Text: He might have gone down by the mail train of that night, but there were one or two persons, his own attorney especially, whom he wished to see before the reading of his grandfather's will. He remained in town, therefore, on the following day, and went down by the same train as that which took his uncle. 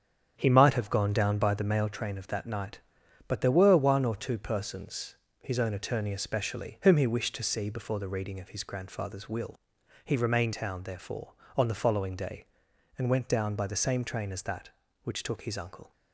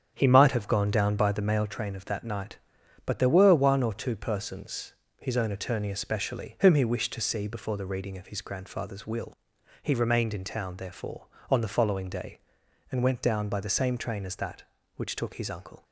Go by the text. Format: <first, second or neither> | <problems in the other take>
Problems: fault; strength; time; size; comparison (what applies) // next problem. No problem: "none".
second | starts louder than the rest; strong; until 1.3 s; 8 dB; strong in the second // skips "in"; at 10.5 s